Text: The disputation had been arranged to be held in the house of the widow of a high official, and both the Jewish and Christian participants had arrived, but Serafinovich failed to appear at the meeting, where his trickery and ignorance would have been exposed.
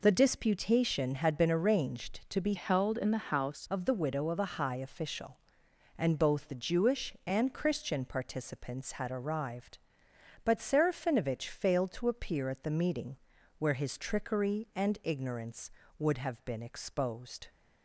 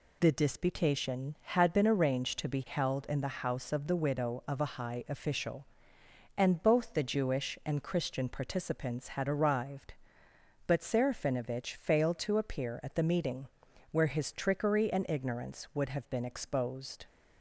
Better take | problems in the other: second | changes voice from "held" to "house"; from 2.5 to 3.6 s; 1.1 s long

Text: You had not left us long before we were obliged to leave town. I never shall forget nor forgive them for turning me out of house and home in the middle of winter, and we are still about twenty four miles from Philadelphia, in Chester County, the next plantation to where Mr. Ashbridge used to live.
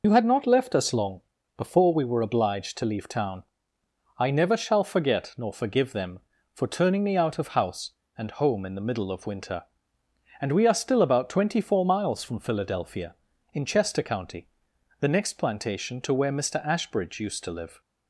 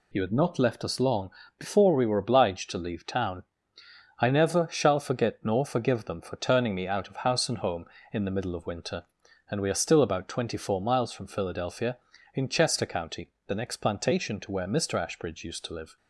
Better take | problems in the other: second | loses the start of "You"; at 0.0 s; 60 ms // pauses between "long" and "before"; slight; at 1.2 s; 0.36 s long; slight in the second

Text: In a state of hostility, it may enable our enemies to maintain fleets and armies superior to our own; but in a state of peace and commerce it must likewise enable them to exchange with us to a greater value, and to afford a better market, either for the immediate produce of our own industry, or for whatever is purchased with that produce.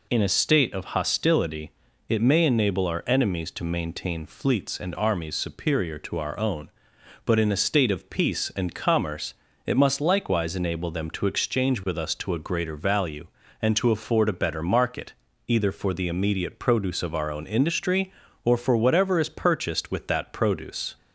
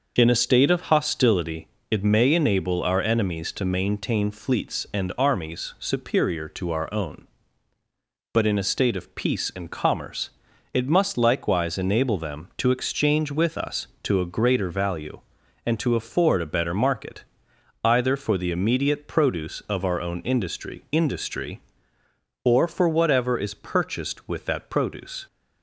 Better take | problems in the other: first | starts louder than the rest; noticeable; until 1.1 s; 6 dB // pauses between "commerce" and "it"; at 10.3 s; 0.42 s long; slight in the first // says "industry" twice; at 20.9 s

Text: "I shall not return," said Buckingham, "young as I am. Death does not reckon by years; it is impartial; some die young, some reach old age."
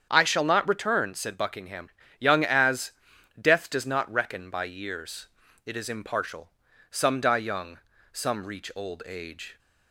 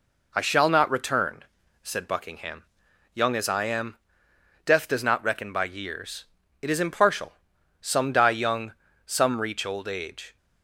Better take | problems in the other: second | starts louder than the rest; strong; until 1.1 s; 8 dB // skips "I am"; at 3.1 s

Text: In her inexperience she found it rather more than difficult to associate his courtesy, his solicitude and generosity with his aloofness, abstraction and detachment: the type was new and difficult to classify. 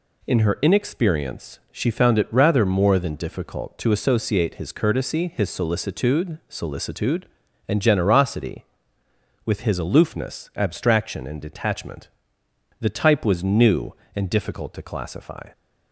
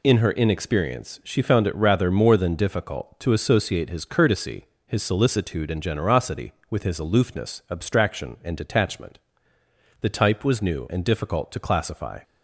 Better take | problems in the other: second | says "solicitude" twice; at 6.4 s

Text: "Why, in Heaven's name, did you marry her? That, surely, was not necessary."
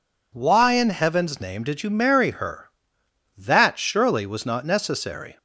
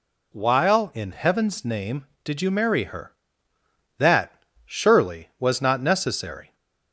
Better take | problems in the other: first | says "While" for "Why"; at 0.3 s

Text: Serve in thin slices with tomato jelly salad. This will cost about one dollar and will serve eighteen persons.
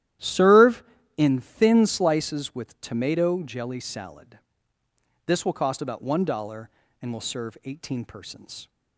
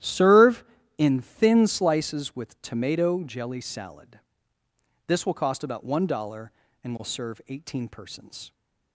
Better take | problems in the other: neither | starts louder than the rest; strong; the same in both

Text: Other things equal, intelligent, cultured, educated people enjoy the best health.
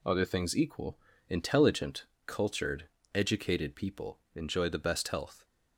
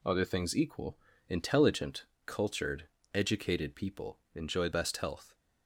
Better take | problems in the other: first | skips "the"; at 4.7 s

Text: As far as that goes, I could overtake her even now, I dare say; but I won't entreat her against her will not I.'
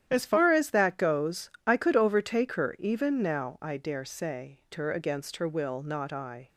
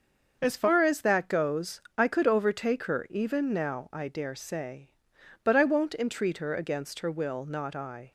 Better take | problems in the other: second | starts louder than the rest; strong; until 1.0 s; 10 dB; also in the second // skips "but I won't entreat"; at 4.6 s

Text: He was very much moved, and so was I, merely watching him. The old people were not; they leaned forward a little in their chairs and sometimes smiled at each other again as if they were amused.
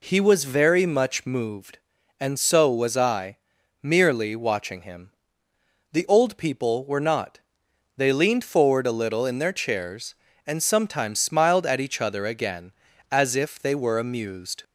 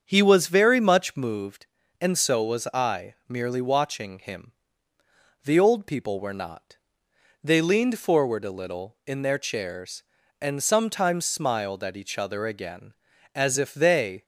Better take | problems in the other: first | starts louder than the rest; strong; until 1.0 s; 7.5 dB // stops before "were amused"; at 14.2 s

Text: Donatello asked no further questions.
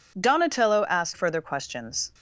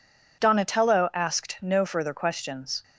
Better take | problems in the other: second | skips "no"; at 1.1 s

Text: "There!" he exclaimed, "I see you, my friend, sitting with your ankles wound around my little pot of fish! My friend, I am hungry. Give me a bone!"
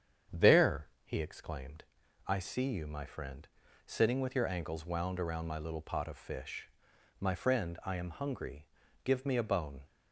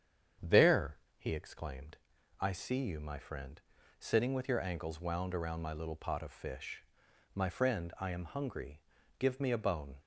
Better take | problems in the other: neither | starts louder than the rest; strong; the same in both

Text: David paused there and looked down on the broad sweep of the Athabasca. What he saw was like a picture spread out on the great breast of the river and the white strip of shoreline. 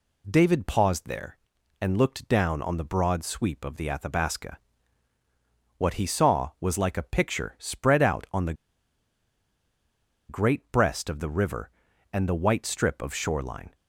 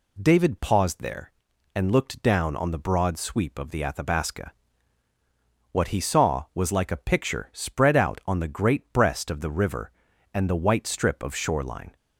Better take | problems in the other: second | pauses between "the" and "great"; strong; at 8.5 s; 1.7 s long

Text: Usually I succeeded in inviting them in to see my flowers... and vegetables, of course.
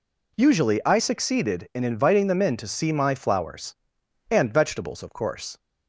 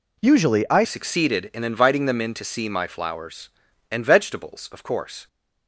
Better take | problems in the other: first | changes voice at "succeeded"; from 0.8 s on; 4.4 s long

